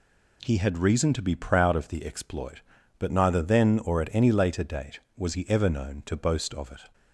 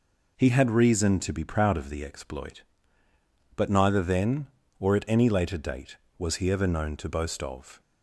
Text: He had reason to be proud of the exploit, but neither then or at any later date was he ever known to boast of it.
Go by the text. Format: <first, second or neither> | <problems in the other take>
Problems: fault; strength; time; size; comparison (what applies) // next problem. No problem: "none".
first | stops before "it"; at 7.7 s